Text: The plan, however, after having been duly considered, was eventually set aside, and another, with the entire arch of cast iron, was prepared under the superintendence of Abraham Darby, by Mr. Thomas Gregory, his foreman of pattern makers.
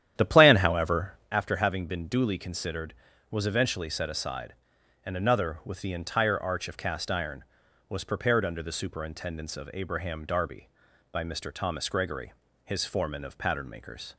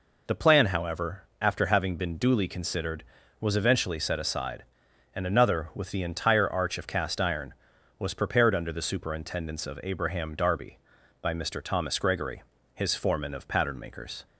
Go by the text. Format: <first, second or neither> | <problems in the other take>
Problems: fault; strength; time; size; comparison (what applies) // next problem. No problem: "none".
second | starts louder than the rest; strong; until 1.3 s; 10.5 dB